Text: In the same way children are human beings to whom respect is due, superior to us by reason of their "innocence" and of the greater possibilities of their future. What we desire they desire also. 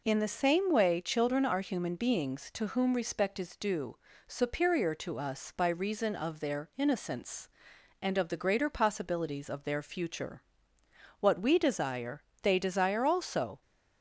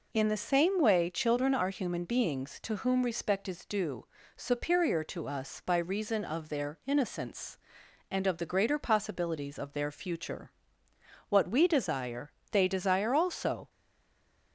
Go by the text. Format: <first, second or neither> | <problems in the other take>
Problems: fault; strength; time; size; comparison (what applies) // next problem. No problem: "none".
first | pauses between "desire" and "they"; slight; at 12.2 s; 0.22 s long; slight in the first // stays silent after the last word; slight; from 13.6 s on; 0.9 s long